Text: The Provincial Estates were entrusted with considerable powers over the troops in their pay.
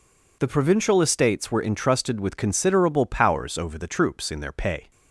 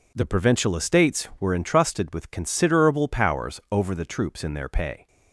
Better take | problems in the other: neither | none

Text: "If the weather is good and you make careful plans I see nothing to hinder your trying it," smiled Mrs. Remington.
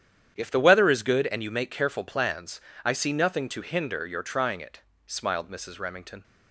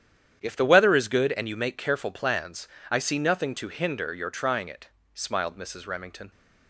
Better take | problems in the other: neither | starts louder than the rest; strong; the same in both // pauses between "plans" and "I"; slight; the same in both

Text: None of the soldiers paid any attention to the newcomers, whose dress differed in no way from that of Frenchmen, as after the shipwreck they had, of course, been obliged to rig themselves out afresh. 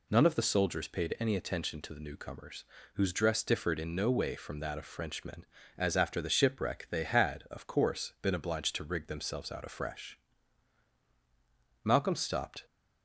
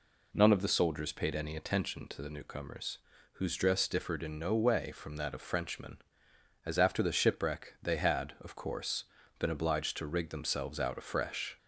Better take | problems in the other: second | goes on to say "Malcolm stopped"; noticeable; from 11.8 s on; 0.82 s long

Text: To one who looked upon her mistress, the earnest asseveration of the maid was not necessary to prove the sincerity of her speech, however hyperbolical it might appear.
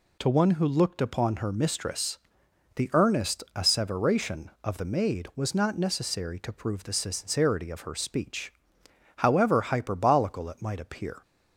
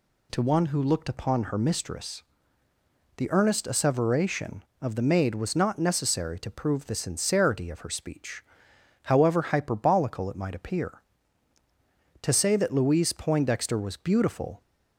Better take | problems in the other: first | goes on to say "To say that Louise Poindexter was beautiful"; strong; from 12.2 s on; 2.4 s long

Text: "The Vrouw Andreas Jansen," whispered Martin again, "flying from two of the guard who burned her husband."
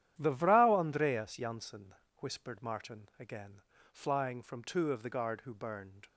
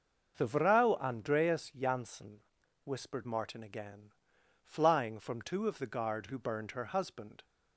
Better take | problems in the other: second | starts louder than the rest; strong; until 1.1 s; 10.5 dB; noticeable in the second // stops before "her husband"; at 6.0 s

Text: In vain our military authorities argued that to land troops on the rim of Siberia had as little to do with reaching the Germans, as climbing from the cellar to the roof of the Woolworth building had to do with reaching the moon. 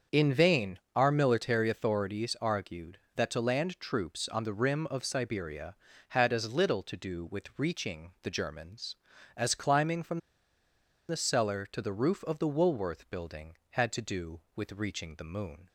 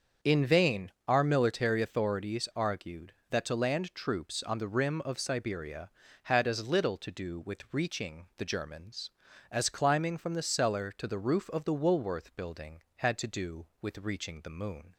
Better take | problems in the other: second | starts louder than the rest; until 1.2 s; 6.5 dB; also in the second // pauses between "vain" and "our"; slight; at 0.7 s; 0.16 s long; slight in the second // pauses between "from" and "the"; noticeable; at 10.1 s; 0.89 s long

